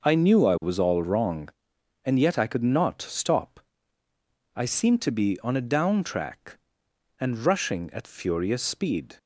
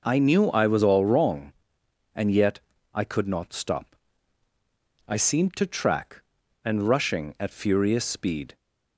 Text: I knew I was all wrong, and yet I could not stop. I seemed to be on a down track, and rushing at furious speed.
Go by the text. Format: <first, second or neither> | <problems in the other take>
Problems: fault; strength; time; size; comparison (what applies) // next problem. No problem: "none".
first | pauses between "yet" and "I"; slight; at 2.5 s; 0.34 s long // skips "be on a down"; at 5.6 s